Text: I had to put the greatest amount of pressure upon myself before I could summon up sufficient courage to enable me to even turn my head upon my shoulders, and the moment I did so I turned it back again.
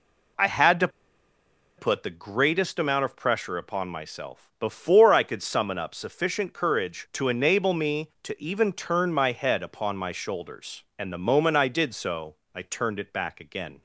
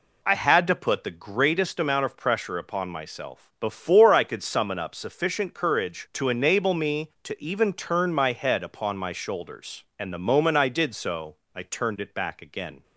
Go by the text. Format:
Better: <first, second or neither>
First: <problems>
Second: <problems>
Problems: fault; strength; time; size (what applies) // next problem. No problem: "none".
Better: second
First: pauses between "to" and "put"; noticeable; at 0.8 s; 0.89 s long // pauses between "so" and "I"; slight; at 12.3 s; 0.18 s long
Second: pauses between "so" and "I"; slight; at 11.3 s; 0.18 s long